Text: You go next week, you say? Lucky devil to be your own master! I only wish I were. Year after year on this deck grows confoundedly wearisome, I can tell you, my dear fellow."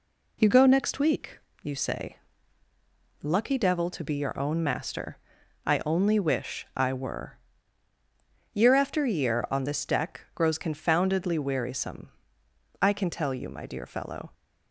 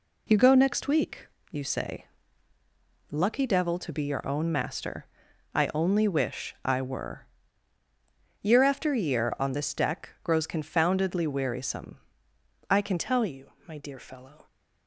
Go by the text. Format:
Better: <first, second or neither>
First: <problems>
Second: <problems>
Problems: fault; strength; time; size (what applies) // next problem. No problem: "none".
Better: first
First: none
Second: changes voice at "tell"; from 12.9 s on; 1.5 s long